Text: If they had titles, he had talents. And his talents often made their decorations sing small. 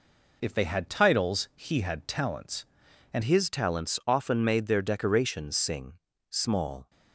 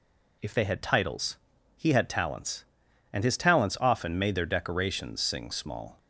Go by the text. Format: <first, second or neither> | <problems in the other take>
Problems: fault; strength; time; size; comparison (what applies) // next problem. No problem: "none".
second | changes voice at "his"; from 3.2 s on; 3.6 s long // pauses between "sing" and "small"; slight; at 5.9 s; 0.36 s long